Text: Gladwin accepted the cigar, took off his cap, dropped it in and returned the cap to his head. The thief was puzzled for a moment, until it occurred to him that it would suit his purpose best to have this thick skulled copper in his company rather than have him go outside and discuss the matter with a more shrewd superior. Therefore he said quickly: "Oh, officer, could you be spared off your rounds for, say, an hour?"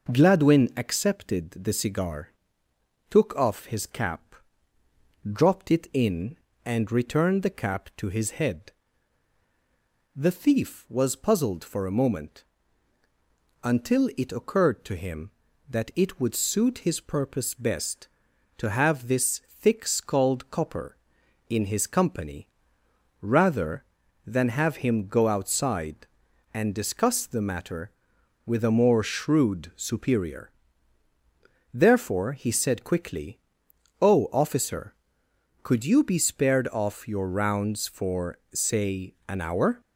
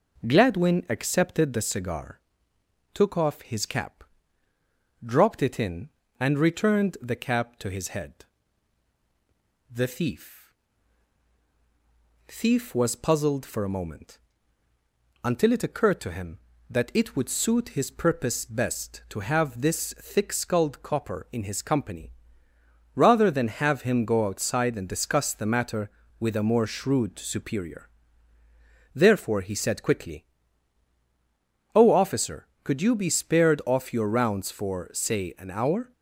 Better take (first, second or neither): first